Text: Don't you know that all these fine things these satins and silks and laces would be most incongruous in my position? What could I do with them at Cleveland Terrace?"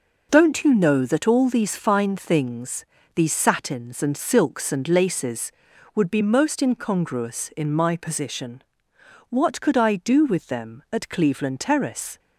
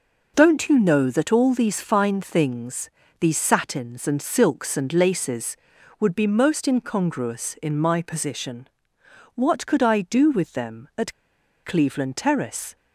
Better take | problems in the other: first | pauses between "things" and "these"; slight; at 2.8 s; 0.32 s long; slight in the first // pauses between "at" and "Cleveland"; noticeable; at 11.1 s; 0.51 s long

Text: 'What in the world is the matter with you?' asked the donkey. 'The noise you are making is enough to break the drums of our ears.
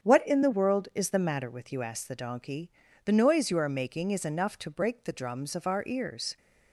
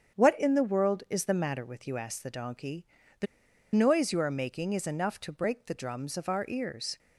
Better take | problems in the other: first | starts louder than the rest; strong; until 1.2 s; 7.5 dB; strong in the first // pauses between "The" and "noise"; noticeable; at 3.2 s; 0.48 s long

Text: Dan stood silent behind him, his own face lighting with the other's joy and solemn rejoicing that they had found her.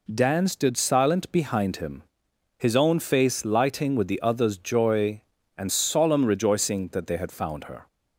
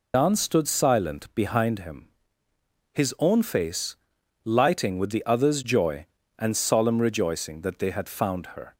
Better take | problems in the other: first | loses the start of "Dan"; at 0.1 s; 125 ms // pauses between "face" and "lighting"; noticeable; at 3.9 s; 0.48 s long

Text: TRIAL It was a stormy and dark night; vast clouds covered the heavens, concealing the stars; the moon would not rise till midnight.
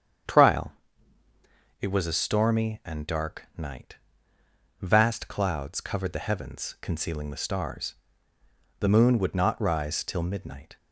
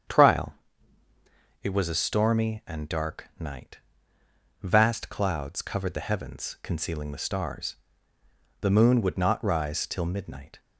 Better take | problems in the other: neither | starts louder than the rest; strong; the same in both // pauses between "TRIAL" and "It"; the same in both

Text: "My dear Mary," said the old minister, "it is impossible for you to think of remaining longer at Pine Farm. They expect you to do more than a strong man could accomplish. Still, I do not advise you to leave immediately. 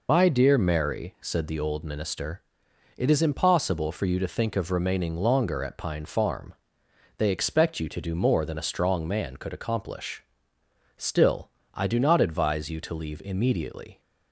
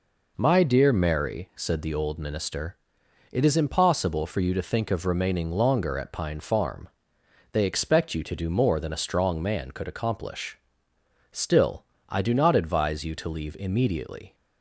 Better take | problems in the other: second | loses the start of "My"; at 0.0 s; 70 ms

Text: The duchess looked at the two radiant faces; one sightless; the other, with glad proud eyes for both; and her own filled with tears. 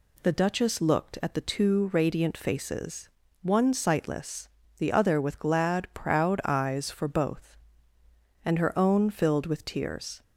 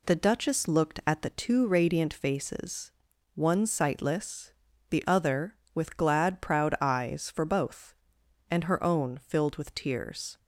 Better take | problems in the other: neither | none

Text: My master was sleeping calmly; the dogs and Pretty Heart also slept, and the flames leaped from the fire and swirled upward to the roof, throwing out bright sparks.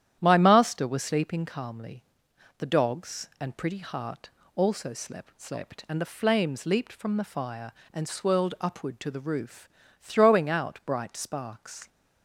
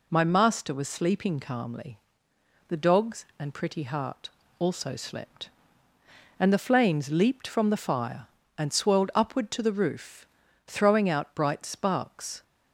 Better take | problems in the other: second | starts louder than the rest; strong; until 1.2 s; 10.5 dB // pauses between "Heart" and "also"; slight; at 4.3 s; 0.26 s long; slight in the second // says "slept" twice; at 5.4 s

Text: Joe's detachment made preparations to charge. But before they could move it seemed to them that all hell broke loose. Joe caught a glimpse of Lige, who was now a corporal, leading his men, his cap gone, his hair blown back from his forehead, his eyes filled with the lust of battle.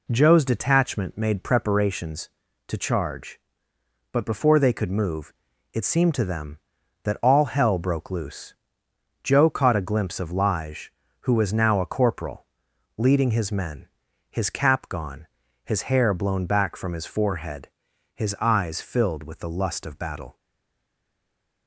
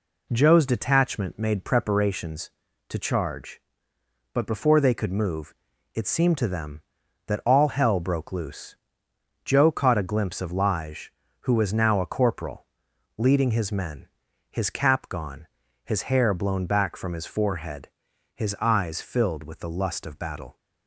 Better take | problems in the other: second | pauses between "move" and "it"; at 5.3 s; 0.40 s long; also in the second // stays silent after the last word; noticeable; from 20.3 s on; 1.3 s long

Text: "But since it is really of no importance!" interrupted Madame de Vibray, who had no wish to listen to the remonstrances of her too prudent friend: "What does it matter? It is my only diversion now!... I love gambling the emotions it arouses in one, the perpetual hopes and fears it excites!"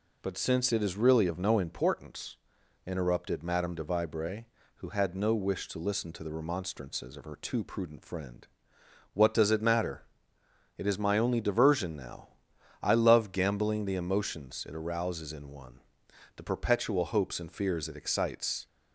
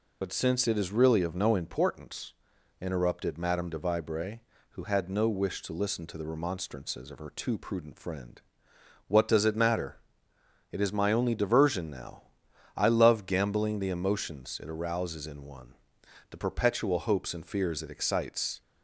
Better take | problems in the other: first | loses the start of "But"; at 0.2 s; 40 ms

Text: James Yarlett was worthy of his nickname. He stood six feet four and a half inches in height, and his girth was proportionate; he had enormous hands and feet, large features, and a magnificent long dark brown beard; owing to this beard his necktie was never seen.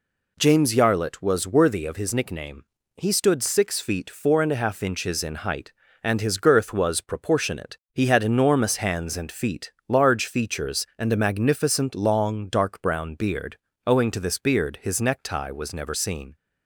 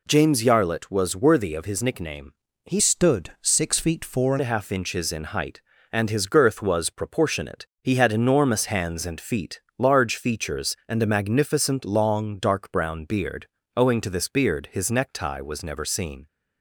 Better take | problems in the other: first | changes voice from "stood" to "and"; from 2.7 to 4.3 s; 1.6 s long

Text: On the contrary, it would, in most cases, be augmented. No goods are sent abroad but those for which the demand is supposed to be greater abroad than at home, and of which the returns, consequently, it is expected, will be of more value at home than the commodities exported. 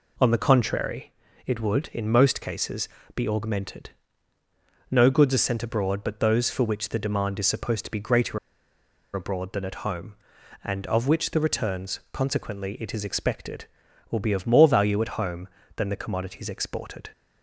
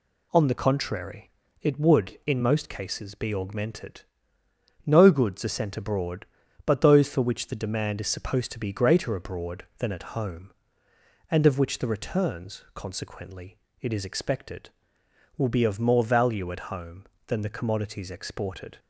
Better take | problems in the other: second | pauses between "greater" and "abroad"; noticeable; at 8.3 s; 0.76 s long

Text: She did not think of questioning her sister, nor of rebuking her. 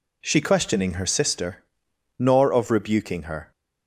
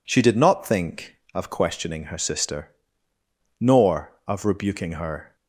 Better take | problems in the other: second | skips "did not think of"; at 0.3 s

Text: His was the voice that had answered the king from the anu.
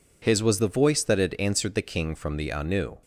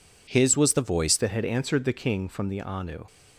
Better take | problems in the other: first | changes voice at "that"; from 1.1 s on; 1.9 s long

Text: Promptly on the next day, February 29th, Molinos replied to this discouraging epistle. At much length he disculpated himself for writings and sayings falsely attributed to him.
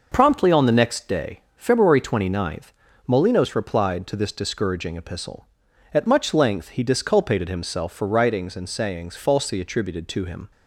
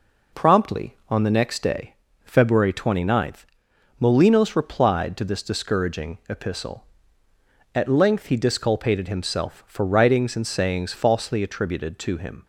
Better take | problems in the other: first | skips "much"; at 7.8 s

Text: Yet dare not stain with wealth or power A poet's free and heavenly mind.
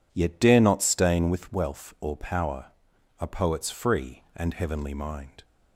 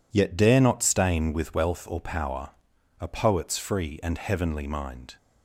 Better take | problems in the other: neither | pauses between "power" and "A"; noticeable; the same in both

